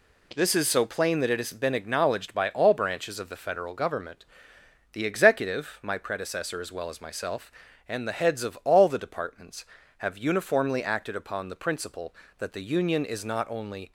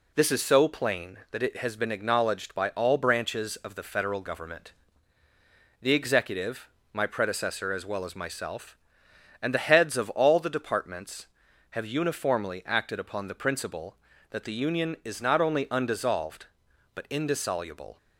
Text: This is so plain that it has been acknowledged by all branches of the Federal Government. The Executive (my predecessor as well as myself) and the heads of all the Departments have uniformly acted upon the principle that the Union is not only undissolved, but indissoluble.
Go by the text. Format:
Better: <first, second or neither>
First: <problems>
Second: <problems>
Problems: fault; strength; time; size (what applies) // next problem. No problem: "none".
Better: second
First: stops before "undissolved but indissoluble"; at 13.8 s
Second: none